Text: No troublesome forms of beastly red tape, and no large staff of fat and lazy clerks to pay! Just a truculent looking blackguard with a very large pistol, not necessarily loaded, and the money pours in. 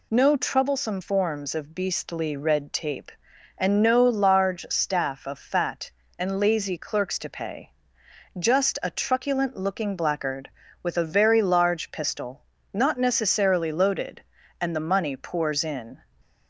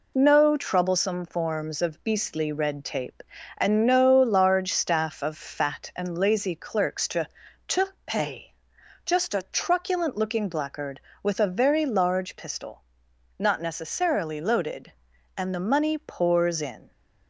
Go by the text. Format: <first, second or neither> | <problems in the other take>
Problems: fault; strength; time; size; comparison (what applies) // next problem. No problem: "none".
first | says "to" twice; at 7.6 s